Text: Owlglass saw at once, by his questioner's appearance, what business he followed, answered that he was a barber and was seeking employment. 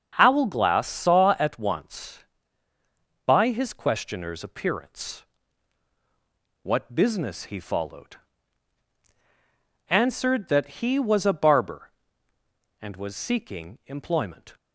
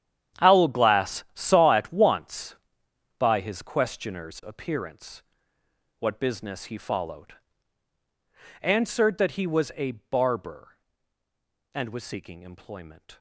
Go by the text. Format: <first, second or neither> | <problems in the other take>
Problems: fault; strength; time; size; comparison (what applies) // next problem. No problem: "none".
first | gets quieter; strong; throughout; 16 dB // starts louder than the rest; strong; until 1.5 s; 9.5 dB; strong in the first